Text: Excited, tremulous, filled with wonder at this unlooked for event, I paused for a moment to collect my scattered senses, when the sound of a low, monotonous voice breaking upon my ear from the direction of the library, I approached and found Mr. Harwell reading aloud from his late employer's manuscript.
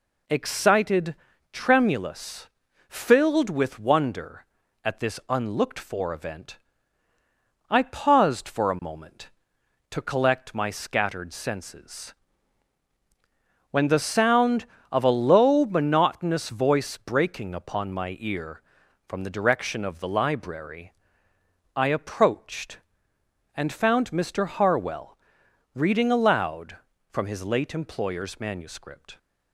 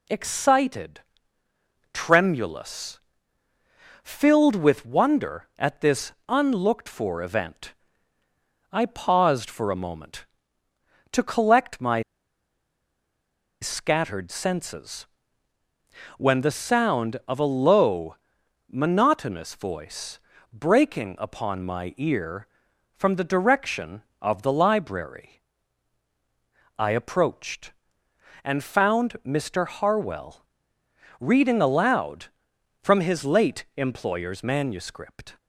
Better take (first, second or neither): first